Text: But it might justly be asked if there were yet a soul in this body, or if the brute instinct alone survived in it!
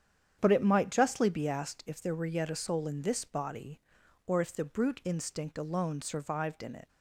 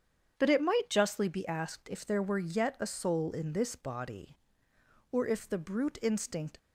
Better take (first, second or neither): first